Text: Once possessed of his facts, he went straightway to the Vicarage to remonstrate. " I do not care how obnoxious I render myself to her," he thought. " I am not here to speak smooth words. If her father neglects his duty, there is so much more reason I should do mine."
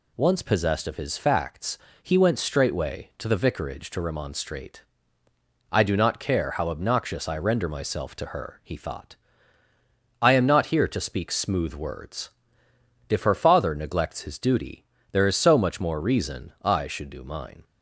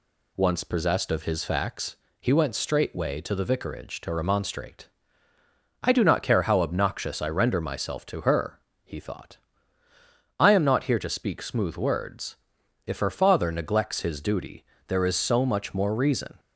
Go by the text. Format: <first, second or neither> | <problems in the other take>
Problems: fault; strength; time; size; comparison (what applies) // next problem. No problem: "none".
first | stops before "I should do mine"; at 16.3 s